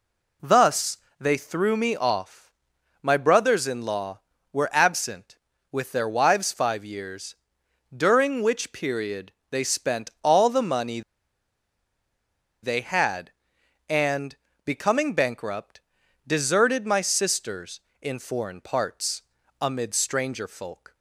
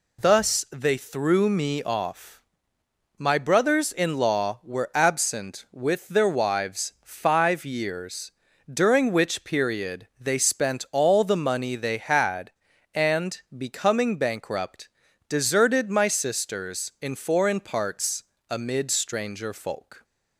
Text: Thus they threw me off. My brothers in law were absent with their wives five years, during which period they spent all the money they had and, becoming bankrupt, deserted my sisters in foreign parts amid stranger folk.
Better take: second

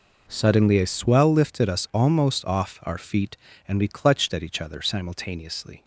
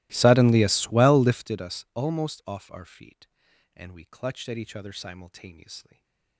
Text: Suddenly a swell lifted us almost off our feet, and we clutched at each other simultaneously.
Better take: first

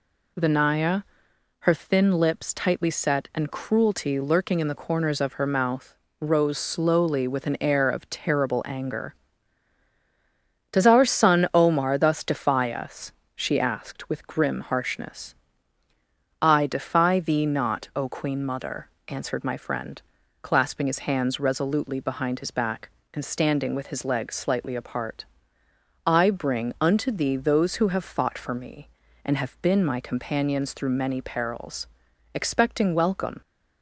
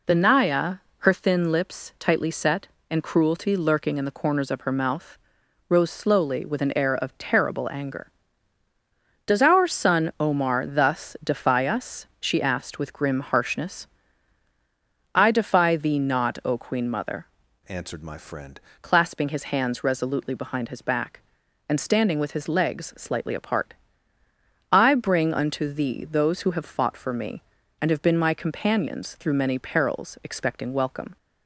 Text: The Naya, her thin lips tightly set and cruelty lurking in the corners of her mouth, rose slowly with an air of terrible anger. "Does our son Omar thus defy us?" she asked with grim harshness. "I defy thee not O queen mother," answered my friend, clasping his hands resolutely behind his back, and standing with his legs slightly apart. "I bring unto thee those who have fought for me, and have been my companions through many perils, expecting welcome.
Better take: first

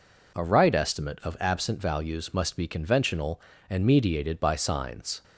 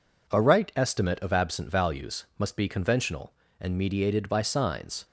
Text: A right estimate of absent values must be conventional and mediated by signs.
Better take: neither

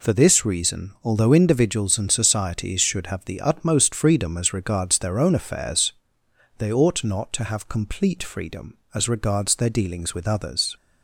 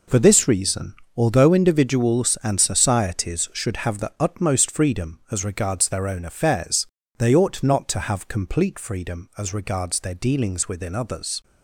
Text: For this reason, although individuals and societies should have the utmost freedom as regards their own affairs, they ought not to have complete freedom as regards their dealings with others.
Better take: first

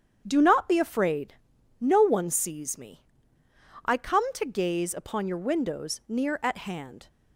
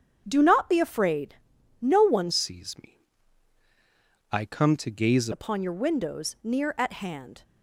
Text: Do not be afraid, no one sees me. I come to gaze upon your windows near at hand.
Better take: first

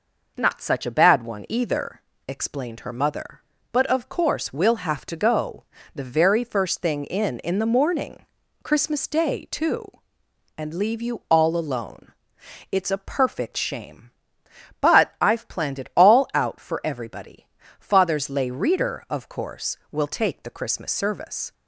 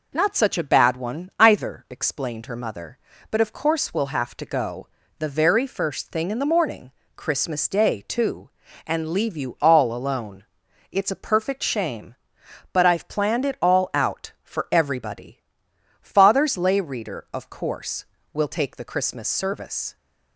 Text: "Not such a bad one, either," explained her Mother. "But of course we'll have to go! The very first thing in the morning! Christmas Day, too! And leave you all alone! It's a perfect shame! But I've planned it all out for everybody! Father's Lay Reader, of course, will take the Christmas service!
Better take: second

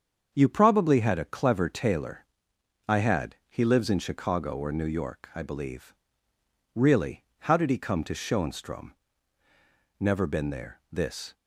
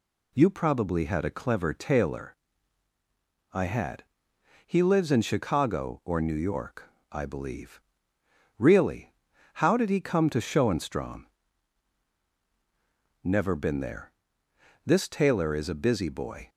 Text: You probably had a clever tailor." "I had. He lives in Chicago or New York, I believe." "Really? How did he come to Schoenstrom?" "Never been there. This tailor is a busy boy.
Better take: second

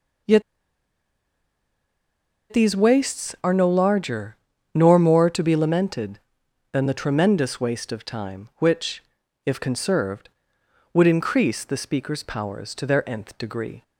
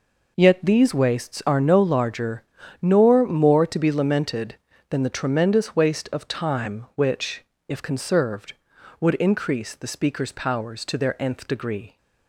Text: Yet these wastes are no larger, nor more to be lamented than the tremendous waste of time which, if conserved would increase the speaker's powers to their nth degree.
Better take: second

